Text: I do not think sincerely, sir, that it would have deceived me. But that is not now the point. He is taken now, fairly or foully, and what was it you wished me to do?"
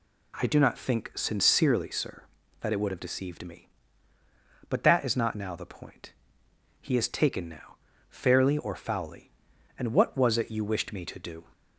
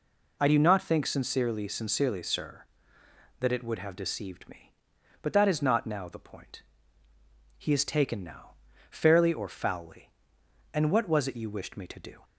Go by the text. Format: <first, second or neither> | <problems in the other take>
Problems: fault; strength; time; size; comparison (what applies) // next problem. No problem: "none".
first | says "sincerely" twice; at 1.6 s